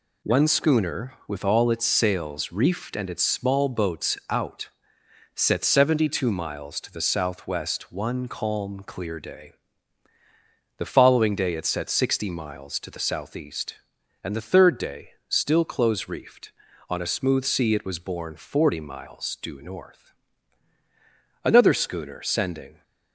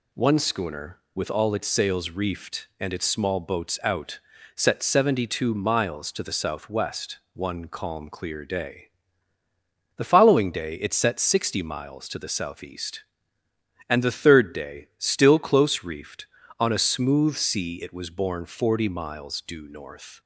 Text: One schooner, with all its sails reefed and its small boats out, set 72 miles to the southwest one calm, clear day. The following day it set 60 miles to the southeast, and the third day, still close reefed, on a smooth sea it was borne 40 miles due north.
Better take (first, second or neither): second